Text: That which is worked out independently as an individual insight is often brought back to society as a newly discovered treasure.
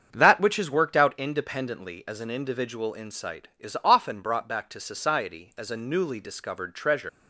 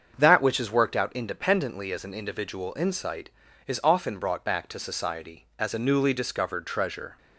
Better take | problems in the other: second | starts louder than the rest; strong; until 1.1 s; 7 dB; also in the second // leaves "treasure" unfinished; at 7.0 s; 120 ms

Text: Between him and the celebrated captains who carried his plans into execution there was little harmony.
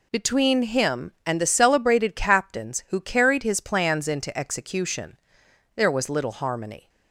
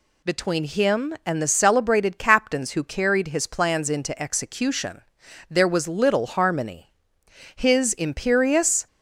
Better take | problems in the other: first | pauses between "execution" and "there"; noticeable; at 5.0 s; 0.48 s long; noticeable in the first // goes on to say "His imperious"; from 7.5 s on; 1.3 s long

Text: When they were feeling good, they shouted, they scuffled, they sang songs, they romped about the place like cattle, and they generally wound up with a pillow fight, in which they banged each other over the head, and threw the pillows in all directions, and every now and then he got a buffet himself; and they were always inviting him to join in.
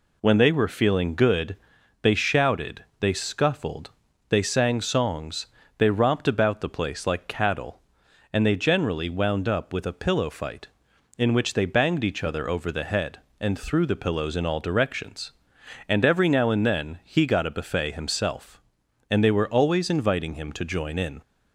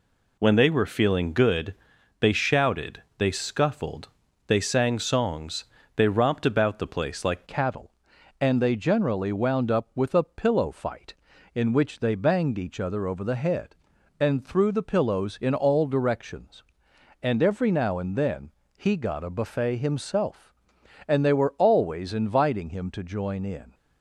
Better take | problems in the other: first | changes voice at "cattle"; from 7.4 s on; 16.3 s long // pauses between "then" and "he"; slight; at 18.4 s; 0.28 s long

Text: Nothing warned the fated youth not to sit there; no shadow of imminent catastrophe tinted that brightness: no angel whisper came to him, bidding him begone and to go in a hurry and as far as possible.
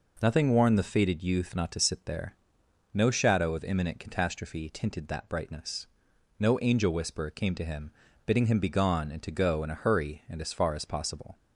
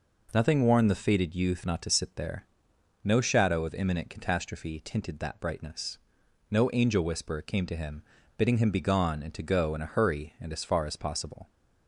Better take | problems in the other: neither | none

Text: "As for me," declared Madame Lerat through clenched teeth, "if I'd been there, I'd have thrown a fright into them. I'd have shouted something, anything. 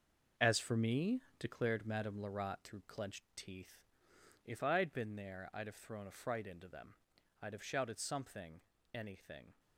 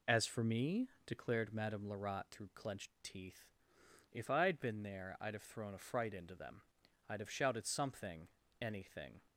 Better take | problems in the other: second | gets quieter; strong; throughout; 9.5 dB

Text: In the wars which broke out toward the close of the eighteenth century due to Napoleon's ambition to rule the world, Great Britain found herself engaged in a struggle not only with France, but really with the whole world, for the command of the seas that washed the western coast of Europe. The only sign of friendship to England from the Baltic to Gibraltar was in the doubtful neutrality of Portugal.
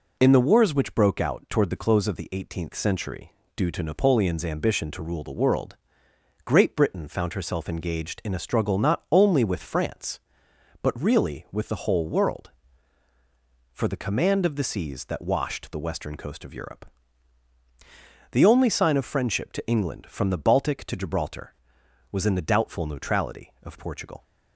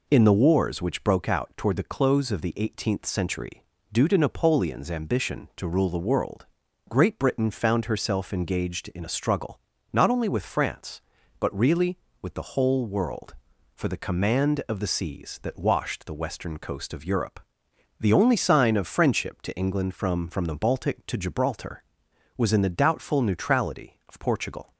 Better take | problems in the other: first | pauses between "century" and "due"; slight; at 3.6 s; 0.28 s long; slight in the first // pauses between "struggle" and "not"; slight; at 9.5 s; 0.34 s long // says "from" twice; at 20.2 s

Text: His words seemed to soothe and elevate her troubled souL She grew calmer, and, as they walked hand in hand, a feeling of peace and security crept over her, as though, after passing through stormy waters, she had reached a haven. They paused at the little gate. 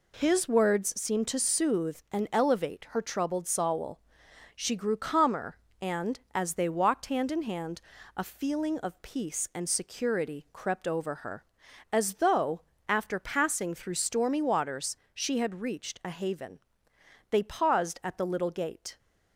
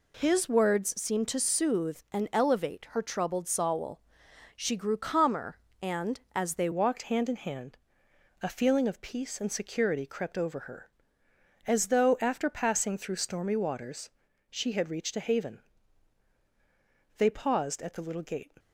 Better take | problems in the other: first | pauses between "souL" and "She"; noticeable; at 3.9 s; 0.56 s long; noticeable in the first // changes voice at "walked"; from 6.7 s on; 11.8 s long

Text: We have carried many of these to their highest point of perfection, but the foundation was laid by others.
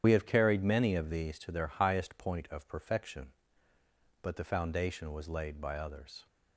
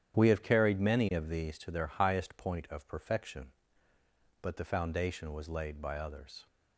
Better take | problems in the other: second | loses the start of "We"; at 0.0 s; 65 ms // starts louder than the rest; strong; until 1.0 s; 9.5 dB; strong in the second

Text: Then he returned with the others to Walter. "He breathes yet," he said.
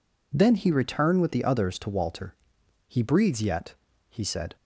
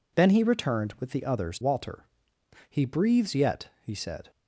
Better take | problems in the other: first | skips "to"; at 1.5 s

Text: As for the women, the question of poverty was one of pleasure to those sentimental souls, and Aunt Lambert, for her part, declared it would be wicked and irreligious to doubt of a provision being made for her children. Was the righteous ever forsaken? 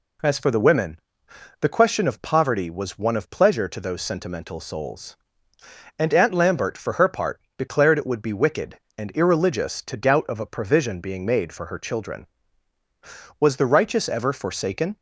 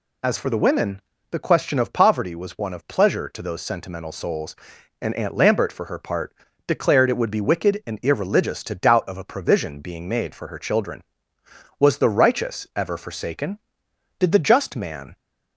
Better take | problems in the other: first | goes on to say "Did the just man"; noticeable; from 14.1 s on; 0.96 s long

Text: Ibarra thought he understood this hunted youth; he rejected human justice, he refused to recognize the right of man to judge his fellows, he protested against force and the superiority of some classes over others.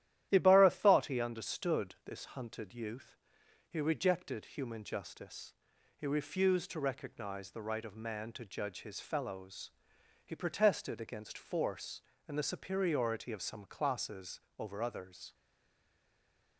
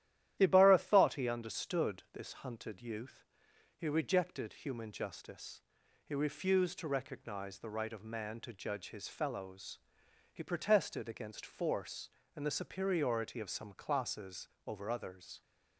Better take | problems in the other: second | starts louder than the rest; strong; until 1.3 s; 12 dB; strong in the second // pauses between "classes" and "over"; slight; at 14.3 s; 0.20 s long; slight in the second // stays silent after the last word; noticeable; from 15.3 s on; 1.2 s long

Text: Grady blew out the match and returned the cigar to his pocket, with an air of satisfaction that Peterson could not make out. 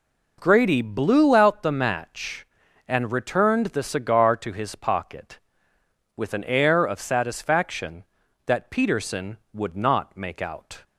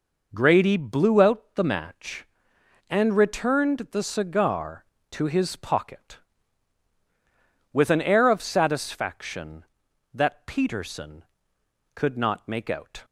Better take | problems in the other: second | says "would" for "could"; at 9.5 s

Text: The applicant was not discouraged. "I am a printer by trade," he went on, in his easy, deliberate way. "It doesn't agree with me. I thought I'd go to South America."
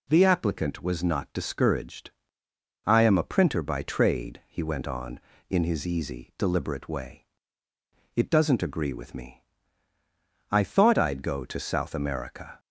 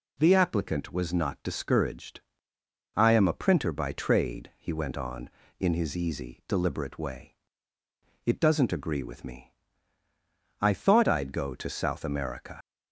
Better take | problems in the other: first | leaves "America" unfinished; at 12.6 s; 85 ms

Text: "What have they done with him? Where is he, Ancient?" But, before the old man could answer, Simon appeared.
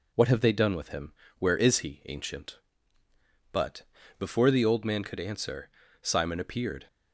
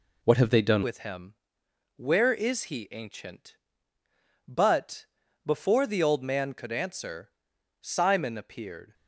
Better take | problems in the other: first | changes voice at "with"; from 0.8 s on; 8.1 s long

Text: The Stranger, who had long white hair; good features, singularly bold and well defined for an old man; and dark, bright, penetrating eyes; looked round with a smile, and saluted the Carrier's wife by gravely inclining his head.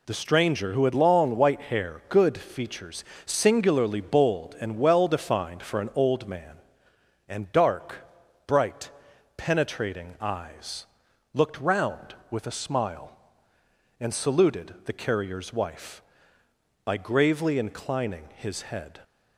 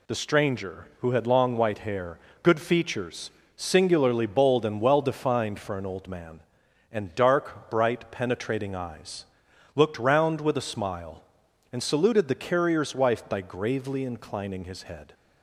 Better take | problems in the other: neither | none

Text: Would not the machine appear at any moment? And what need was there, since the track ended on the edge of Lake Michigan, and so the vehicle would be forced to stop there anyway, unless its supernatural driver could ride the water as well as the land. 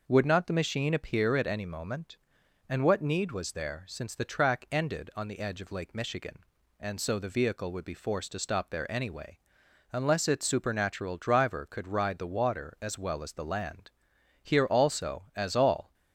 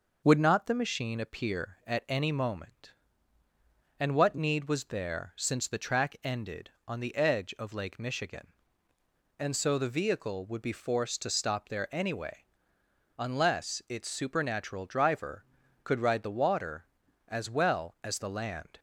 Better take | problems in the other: second | goes on to say "Here also as all"; from 14.4 s on; 1.5 s long

